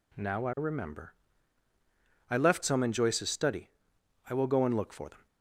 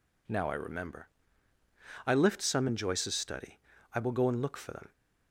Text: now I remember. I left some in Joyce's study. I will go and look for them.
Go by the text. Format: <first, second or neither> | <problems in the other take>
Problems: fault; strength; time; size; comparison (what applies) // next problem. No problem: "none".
first | says "lift" for "left"; at 2.1 s